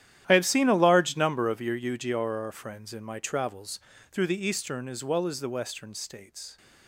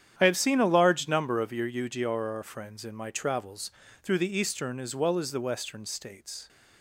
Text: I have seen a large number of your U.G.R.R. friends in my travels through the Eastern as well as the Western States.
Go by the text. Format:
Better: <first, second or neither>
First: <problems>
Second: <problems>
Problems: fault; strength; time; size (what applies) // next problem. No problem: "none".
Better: second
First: gets quieter; strong; throughout; 15 dB // starts louder than the rest; strong; until 1.2 s; 11.5 dB // pauses between "travels" and "through"; slight; at 3.7 s; 0.32 s long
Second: starts louder than the rest; strong; until 1.1 s; 9.5 dB // pauses between "travels" and "through"; slight; at 3.7 s; 0.32 s long